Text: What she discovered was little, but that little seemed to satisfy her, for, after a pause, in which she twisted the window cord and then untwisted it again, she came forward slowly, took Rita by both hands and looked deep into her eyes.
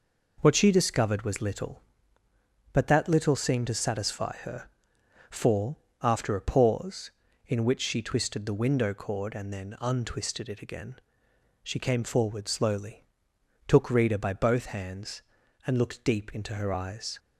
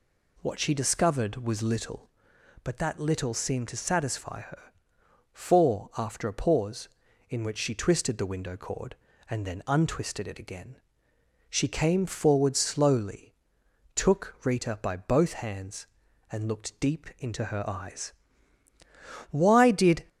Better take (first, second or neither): first